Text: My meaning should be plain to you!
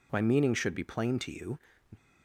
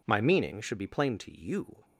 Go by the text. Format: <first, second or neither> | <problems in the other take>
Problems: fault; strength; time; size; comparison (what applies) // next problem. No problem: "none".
neither | none